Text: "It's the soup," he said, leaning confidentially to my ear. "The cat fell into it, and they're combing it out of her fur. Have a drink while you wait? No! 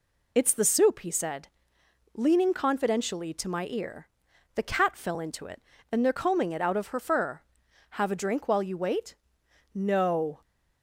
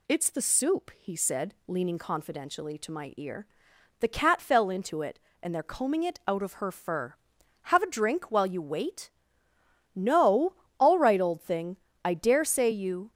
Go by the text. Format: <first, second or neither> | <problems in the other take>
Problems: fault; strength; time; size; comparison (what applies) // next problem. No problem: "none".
first | goes on to say "All right old thing I dare say you"; strong; from 10.7 s on; 2.3 s long